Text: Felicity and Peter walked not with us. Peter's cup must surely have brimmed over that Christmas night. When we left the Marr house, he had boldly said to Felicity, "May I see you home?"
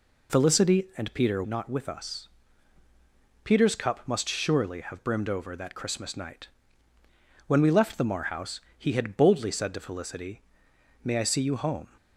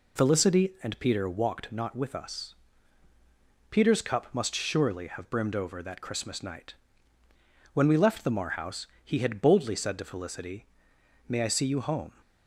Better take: second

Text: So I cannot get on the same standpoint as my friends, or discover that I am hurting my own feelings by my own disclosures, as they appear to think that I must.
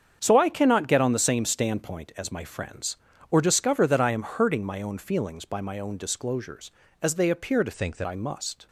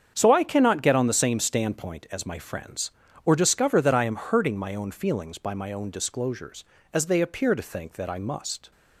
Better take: second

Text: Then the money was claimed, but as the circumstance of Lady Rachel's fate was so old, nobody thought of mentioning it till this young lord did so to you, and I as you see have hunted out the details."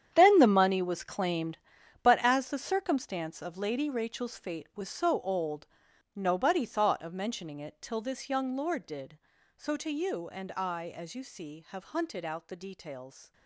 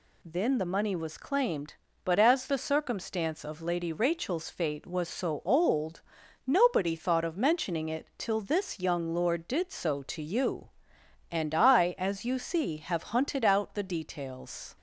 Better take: second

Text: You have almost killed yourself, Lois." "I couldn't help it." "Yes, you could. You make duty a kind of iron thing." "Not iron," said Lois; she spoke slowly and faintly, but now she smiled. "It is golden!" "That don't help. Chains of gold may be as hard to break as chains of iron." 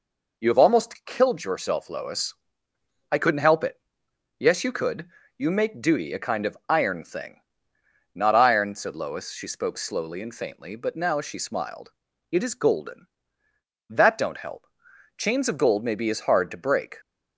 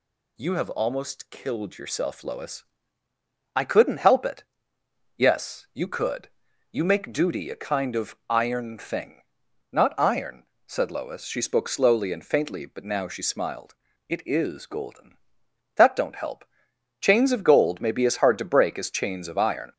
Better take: second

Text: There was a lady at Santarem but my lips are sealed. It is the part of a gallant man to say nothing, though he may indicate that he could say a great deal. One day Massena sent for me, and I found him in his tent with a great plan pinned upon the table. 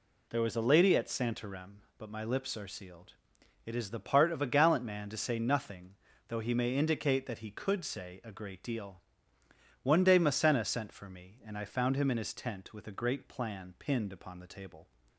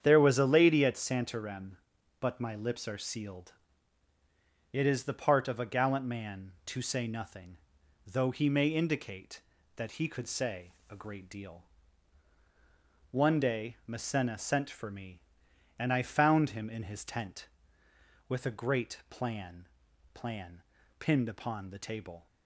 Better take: first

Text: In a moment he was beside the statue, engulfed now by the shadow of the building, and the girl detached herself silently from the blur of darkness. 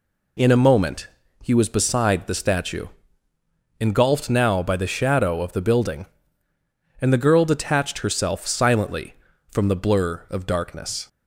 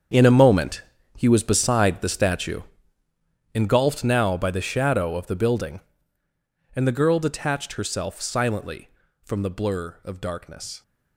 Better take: first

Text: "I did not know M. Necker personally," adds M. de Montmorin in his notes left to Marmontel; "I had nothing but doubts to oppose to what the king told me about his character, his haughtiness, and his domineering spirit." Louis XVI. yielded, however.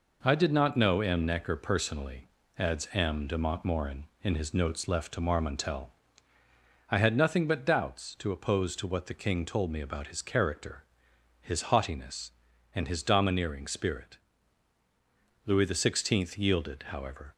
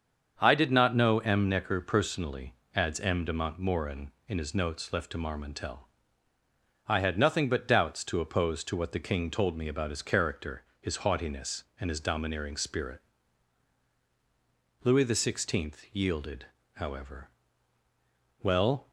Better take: first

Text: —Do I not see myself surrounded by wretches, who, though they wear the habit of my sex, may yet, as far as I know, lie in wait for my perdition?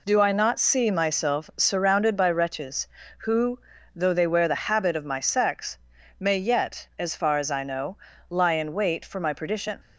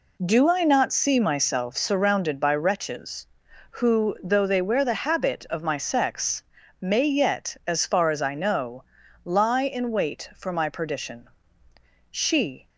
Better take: first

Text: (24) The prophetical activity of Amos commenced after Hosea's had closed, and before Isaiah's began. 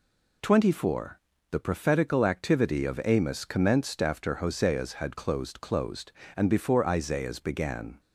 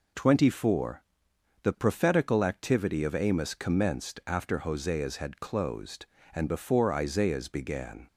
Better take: second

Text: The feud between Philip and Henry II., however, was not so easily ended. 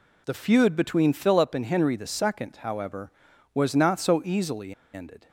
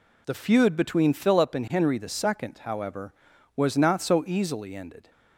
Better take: second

